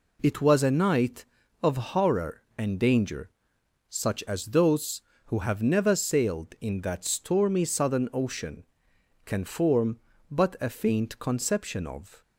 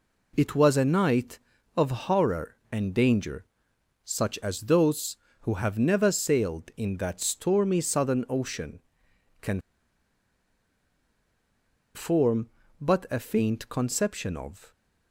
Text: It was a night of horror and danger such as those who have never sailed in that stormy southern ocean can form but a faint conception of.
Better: first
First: pauses between "danger" and "such"; noticeable; at 3.2 s; 0.60 s long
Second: pauses between "danger" and "such"; noticeable; at 3.4 s; 0.60 s long // pauses between "can" and "form"; strong; at 9.6 s; 2.3 s long

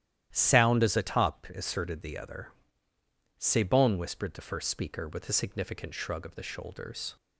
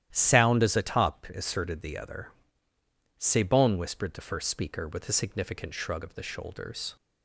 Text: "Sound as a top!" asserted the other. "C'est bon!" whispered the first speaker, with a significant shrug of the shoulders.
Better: neither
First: starts louder than the rest; strong; until 1.3 s; 11.5 dB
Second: starts louder than the rest; strong; until 1.1 s; 11.5 dB

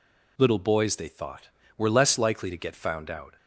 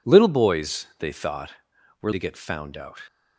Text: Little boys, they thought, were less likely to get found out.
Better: first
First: none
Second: skips "less likely"; at 2.1 s

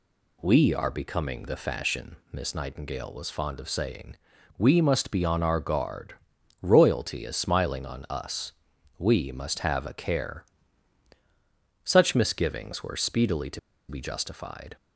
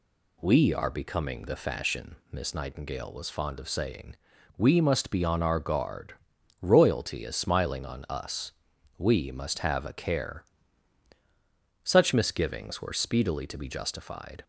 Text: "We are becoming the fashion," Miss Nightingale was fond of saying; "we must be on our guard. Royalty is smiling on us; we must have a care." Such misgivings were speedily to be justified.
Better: second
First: pauses between "to" and "be"; slight; at 13.5 s; 0.30 s long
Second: none

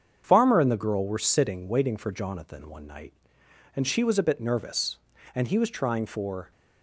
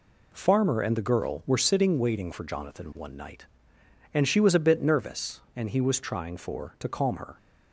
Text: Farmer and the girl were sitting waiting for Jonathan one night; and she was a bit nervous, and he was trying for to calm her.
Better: second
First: starts louder than the rest; until 1.2 s; 7 dB // stops before "to calm her"; at 6.5 s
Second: none

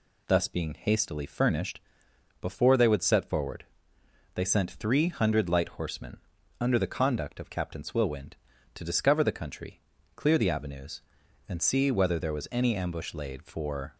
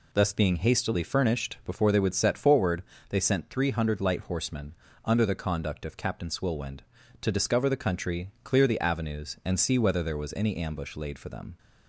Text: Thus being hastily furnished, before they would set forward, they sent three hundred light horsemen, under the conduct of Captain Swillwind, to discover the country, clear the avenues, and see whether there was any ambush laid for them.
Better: second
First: stops before "them"; at 13.9 s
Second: none

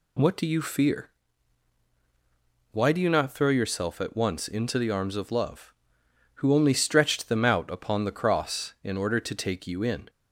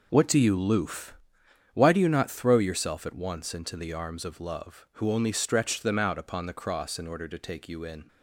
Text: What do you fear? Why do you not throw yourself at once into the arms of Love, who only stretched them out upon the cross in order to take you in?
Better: first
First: none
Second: says "loof" for "fear"; at 0.5 s

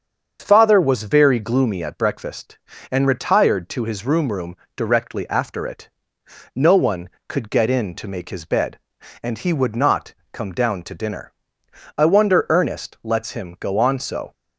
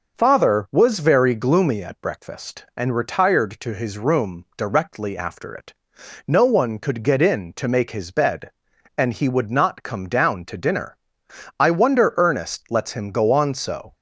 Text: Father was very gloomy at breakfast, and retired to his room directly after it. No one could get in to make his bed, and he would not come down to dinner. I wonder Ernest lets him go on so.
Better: second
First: starts louder than the rest; until 1.4 s; 7 dB // says "room" twice; at 4.3 s // pauses between "not" and "come"; slight; at 10.1 s; 0.18 s long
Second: none

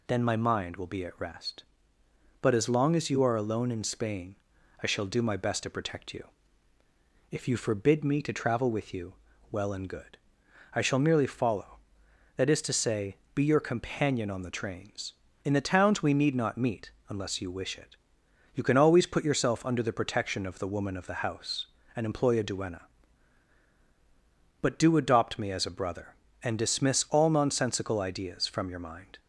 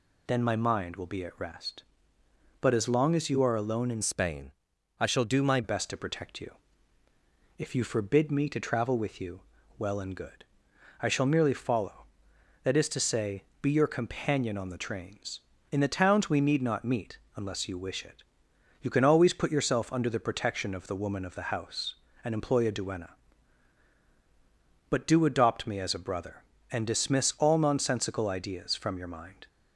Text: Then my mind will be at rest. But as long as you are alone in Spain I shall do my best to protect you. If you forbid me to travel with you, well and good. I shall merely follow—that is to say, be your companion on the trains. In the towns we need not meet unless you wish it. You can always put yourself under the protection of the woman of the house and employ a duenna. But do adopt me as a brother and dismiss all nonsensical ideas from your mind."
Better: first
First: pauses between "Spain" and "I"; noticeable; at 4.3 s; 0.46 s long // pauses between "meet" and "unless"; slight; at 16.9 s; 0.18 s long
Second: changes voice from "Spain" to "my"; from 4.0 to 5.6 s; 1.6 s long // pauses between "Spain" and "I"; noticeable; at 4.5 s; 0.50 s long // pauses between "meet" and "unless"; slight; at 17.1 s; 0.18 s long

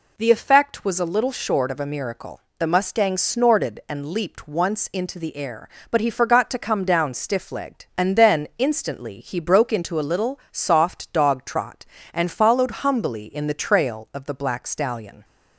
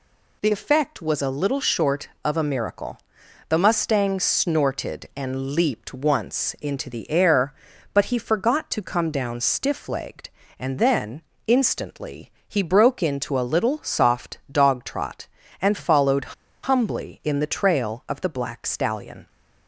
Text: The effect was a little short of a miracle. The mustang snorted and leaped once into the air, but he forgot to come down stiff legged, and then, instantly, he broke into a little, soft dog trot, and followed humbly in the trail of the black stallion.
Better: first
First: none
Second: pauses between "followed" and "humbly"; slight; at 16.3 s; 0.29 s long

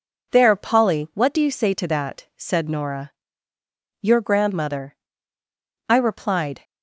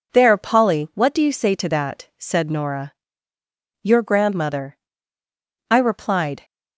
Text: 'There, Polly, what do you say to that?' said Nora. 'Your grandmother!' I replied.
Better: neither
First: none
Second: none

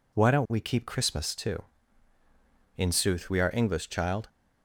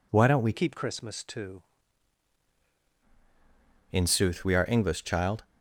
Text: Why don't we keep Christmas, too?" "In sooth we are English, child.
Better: first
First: none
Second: changes voice from "keep" to "too"; from 0.5 to 1.6 s; 1.1 s long

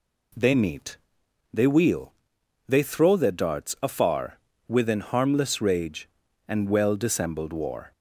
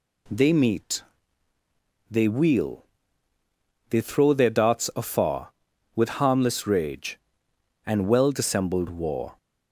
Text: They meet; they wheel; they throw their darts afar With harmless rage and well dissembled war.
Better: second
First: says "Within" for "With"; at 4.6 s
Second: none

